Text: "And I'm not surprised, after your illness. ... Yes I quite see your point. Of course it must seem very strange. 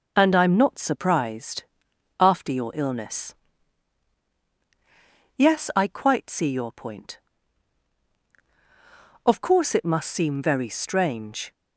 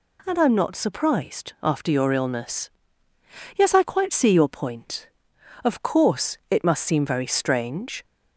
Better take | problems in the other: neither | none

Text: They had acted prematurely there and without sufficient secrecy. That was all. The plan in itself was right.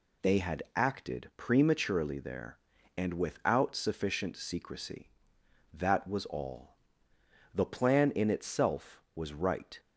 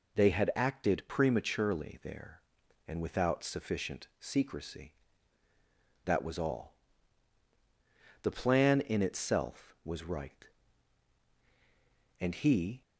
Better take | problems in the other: first | goes on to say "And he"; noticeable; from 12.1 s on; 0.62 s long

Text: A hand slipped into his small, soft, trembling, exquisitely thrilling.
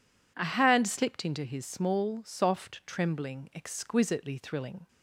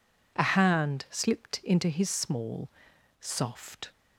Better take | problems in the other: first | stops before "trembling exquisitely thrilling"; at 3.9 s

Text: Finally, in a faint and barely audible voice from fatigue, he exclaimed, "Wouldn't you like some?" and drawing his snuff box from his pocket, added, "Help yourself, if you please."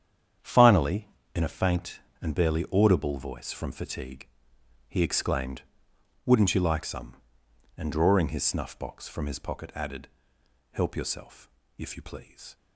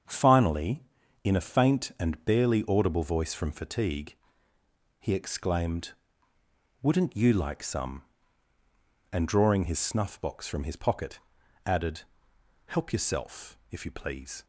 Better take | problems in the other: second | gets quieter; strong; throughout; 10.5 dB // starts louder than the rest; strong; until 1.6 s; 8.5 dB; also in the second

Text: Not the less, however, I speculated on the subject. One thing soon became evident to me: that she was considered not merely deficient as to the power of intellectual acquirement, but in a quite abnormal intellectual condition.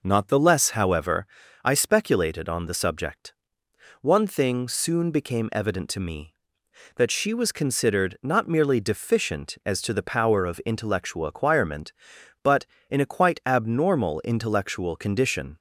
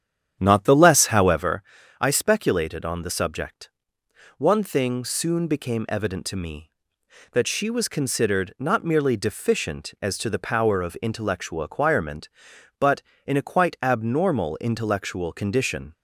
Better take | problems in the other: first | starts louder than the rest; strong; until 1.4 s; 9 dB

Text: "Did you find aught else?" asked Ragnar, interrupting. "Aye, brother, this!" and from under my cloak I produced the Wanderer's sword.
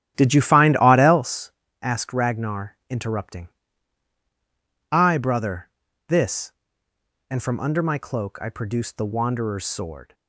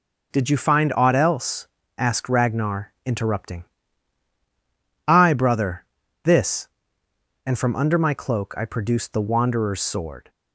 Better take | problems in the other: second | starts louder than the rest; strong; until 1.4 s; 10.5 dB

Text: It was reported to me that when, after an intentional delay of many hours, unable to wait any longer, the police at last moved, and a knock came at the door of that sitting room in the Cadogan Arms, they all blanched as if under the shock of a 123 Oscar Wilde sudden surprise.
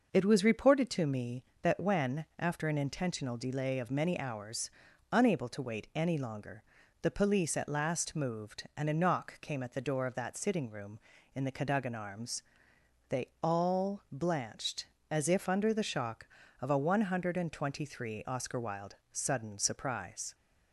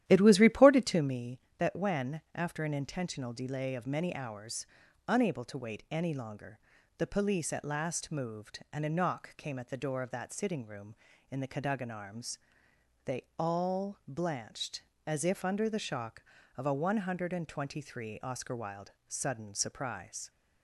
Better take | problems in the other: first | starts louder than the rest; strong; until 1.2 s; 12 dB // pauses between "they" and "all"; slight; at 13.2 s; 0.16 s long; slight in the first // pauses between "Wilde" and "sudden"; slight; at 18.9 s; 0.16 s long; slight in the first

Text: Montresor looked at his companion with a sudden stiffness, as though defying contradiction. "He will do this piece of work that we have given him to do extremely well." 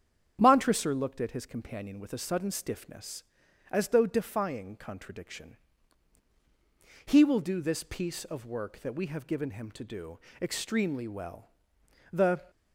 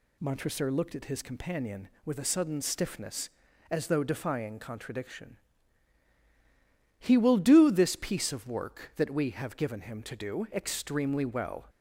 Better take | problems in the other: second | starts louder than the rest; strong; until 1.4 s; 8.5 dB // pauses between "do" and "extremely"; slight; at 10.1 s; 0.22 s long // goes on to say "The"; slight; from 12.0 s on; 0.40 s long

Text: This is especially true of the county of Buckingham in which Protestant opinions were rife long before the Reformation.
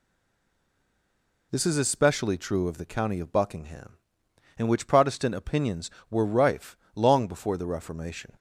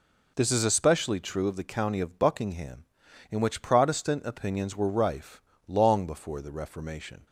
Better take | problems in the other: second | stays silent before the first word; noticeable; until 1.5 s; 1.5 s long // pauses between "rife" and "long"; slight; at 6.7 s; 0.18 s long; slight in the second

